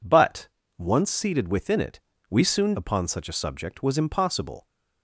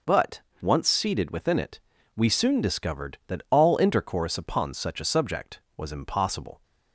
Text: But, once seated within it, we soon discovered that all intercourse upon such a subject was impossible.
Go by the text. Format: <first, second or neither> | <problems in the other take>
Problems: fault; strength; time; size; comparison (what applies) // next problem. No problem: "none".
second | skips "discovered that all intercourse"; at 2.7 s